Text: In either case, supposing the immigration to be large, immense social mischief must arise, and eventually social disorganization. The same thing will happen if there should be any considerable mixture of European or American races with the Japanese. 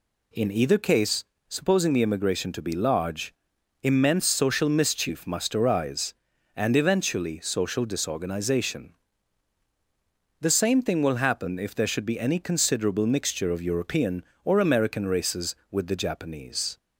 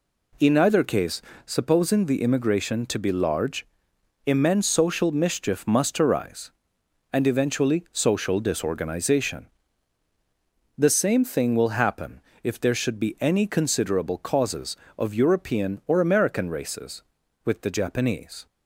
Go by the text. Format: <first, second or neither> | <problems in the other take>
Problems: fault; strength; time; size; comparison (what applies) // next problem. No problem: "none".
first | pauses between "happen" and "if"; slight; at 12.1 s; 0.22 s long // says "causes" for "mixture"; at 14.1 s